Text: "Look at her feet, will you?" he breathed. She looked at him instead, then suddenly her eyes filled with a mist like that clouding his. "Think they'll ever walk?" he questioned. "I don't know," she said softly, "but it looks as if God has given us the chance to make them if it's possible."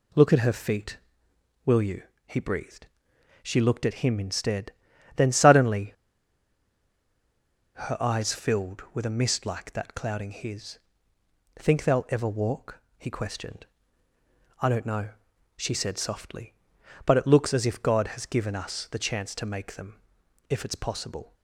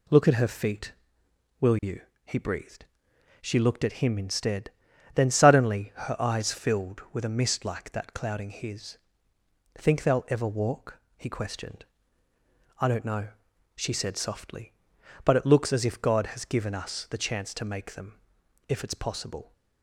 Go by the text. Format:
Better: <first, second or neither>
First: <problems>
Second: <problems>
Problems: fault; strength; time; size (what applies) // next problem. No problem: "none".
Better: second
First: pauses between "suddenly" and "her"; strong; at 5.9 s; 1.8 s long // pauses between "them" and "if"; noticeable; at 19.9 s; 0.48 s long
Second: pauses between "them" and "if"; noticeable; at 18.1 s; 0.48 s long